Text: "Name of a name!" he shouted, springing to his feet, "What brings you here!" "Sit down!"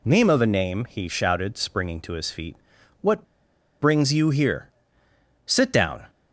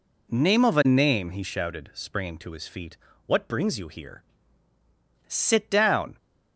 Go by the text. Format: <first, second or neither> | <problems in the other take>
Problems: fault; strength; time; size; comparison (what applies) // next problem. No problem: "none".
second | pauses between "What" and "brings"; noticeable; at 3.2 s; 0.56 s long